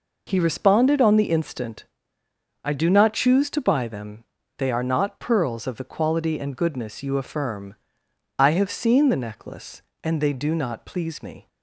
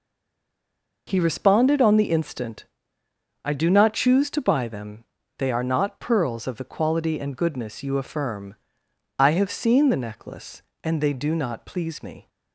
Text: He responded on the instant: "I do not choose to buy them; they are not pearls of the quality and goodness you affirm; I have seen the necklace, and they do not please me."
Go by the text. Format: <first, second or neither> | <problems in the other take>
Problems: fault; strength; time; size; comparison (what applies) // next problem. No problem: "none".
first | stays silent before the first word; until 1.0 s; 1.0 s long